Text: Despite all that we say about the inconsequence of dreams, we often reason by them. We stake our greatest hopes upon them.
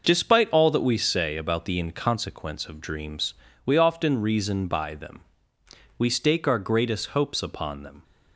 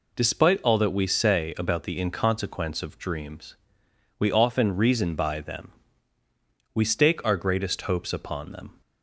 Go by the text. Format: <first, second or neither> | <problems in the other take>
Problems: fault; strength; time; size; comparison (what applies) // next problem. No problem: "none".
neither | none